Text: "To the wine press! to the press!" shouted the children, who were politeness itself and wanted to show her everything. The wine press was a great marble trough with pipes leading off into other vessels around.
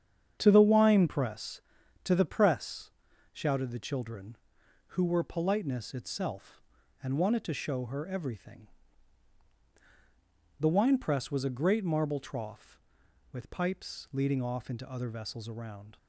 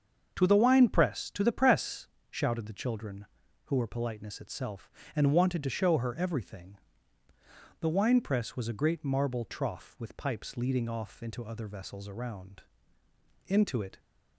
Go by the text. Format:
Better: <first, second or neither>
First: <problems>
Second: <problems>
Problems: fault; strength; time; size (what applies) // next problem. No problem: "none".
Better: first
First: starts louder than the rest; strong; until 1.4 s; 8 dB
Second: starts louder than the rest; until 1.3 s; 6.5 dB // goes on to say "Into it"; from 13.4 s on; 0.52 s long